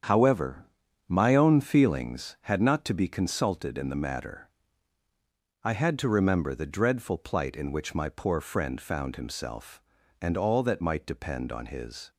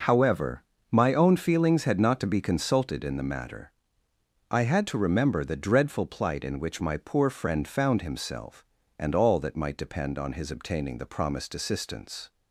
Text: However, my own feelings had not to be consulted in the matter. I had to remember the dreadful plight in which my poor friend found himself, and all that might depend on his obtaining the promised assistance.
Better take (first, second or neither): second